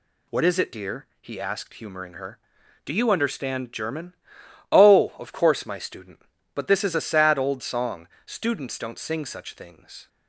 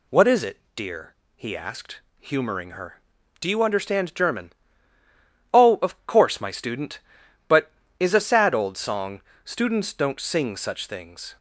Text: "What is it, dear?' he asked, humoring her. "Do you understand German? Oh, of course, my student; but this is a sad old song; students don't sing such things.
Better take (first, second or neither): first